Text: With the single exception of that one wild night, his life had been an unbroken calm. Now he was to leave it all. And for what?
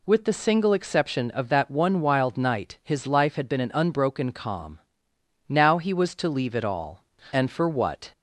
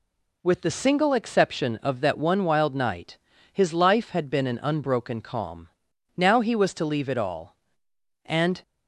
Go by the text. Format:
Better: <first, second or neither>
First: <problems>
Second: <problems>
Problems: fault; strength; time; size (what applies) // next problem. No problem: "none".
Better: first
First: none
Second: stops before "for what"; at 8.6 s